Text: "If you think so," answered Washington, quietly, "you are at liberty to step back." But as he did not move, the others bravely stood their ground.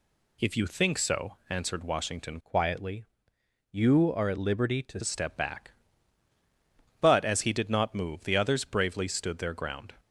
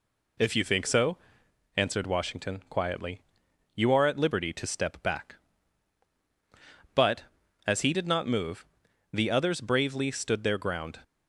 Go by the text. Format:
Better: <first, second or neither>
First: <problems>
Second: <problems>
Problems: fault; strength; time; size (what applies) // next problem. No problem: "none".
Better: second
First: changes voice from "quietly" to "to"; from 2.4 to 4.9 s; 2.5 s long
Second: none